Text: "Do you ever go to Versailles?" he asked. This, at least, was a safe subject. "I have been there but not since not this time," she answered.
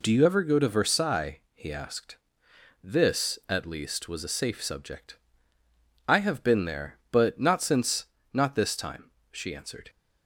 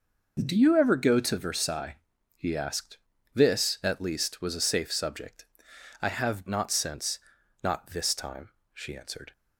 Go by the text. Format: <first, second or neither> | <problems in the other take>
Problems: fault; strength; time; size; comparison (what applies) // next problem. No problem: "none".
first | skips "been there but"; at 6.4 s // pauses between "since" and "not"; at 7.1 s; 0.42 s long; slight in the first